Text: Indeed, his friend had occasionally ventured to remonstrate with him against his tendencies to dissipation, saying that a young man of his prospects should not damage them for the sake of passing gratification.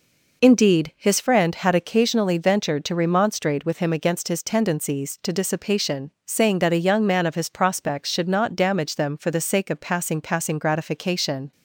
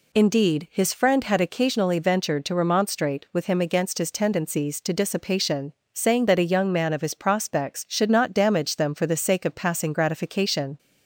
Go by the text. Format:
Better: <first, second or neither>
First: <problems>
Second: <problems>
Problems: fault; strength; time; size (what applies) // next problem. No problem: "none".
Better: second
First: says "passing" twice; at 10.1 s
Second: none